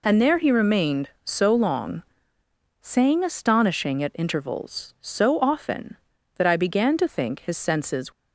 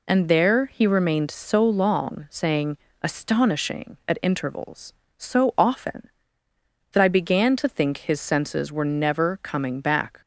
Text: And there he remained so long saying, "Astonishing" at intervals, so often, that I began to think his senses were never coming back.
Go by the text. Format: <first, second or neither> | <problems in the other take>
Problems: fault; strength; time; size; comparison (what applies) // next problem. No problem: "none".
second | pauses between "long" and "saying"; noticeable; at 2.0 s; 0.80 s long // stops before "were never coming back"; at 8.1 s